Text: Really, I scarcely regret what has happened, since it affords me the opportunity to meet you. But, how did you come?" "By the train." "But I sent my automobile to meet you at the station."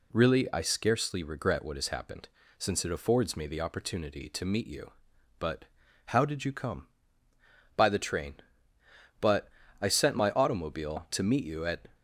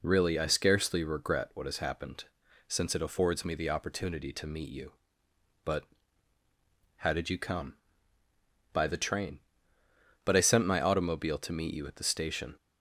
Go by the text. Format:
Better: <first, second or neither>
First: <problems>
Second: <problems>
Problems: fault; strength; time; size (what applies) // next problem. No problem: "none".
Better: second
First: pauses between "But" and "I"; slight; at 9.4 s; 0.30 s long // stops before "the station"; at 11.9 s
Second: none